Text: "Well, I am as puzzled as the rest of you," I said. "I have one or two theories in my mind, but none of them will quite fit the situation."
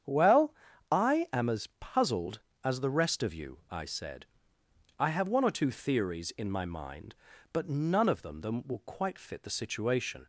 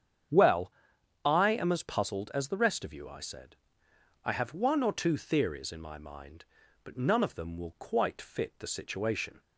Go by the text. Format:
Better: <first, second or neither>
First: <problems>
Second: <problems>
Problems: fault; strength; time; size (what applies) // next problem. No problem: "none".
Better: second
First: starts louder than the rest; strong; until 1.5 s; 8.5 dB // says "them" twice; at 8.4 s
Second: starts louder than the rest; strong; until 1.8 s; 8 dB